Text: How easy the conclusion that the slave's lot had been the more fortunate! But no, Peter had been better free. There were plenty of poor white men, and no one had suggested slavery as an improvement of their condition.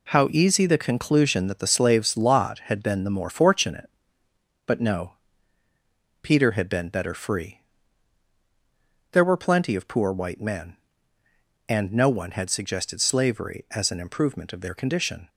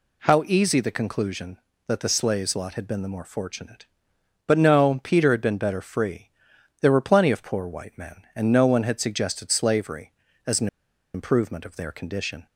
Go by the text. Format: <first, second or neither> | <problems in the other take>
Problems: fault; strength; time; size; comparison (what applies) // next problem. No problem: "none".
first | pauses between "an" and "improvement"; noticeable; at 10.6 s; 0.47 s long